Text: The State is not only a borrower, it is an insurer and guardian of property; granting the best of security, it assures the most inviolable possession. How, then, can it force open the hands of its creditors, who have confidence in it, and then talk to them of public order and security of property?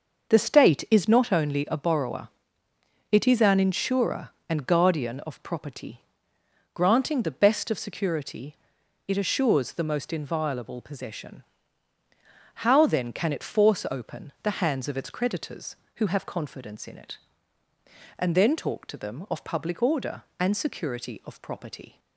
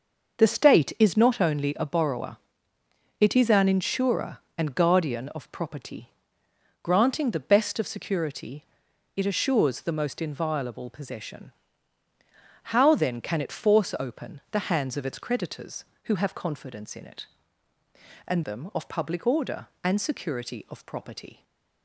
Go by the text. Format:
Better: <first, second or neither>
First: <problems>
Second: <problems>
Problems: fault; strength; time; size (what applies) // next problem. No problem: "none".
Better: first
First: starts louder than the rest; noticeable; until 1.3 s; 6 dB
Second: starts louder than the rest; noticeable; until 1.4 s; 6 dB // skips "then talk to"; at 18.4 s // stays silent after the last word; slight; from 21.3 s on; 0.5 s long